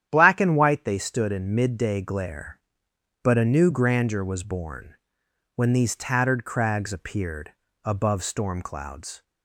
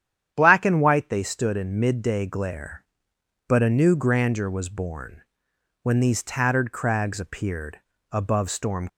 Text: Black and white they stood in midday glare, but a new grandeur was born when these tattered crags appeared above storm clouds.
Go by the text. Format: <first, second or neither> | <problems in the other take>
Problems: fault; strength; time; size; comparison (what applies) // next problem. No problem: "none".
first | starts louder than the rest; strong; until 1.3 s; 9.5 dB; strong in the first // pauses between "born" and "when"; noticeable; at 5.2 s; 0.58 s long; noticeable in the first // pauses between "appeared" and "above"; slight; at 7.8 s; 0.30 s long; slight in the first // stops before "clouds"; at 8.8 s